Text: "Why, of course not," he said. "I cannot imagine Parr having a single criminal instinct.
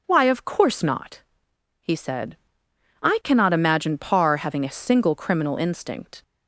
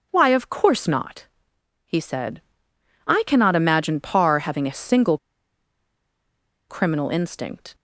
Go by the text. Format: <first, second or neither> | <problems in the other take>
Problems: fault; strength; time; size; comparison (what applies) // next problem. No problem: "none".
first | pauses between "single" and "criminal"; strong; at 5.1 s; 1.5 s long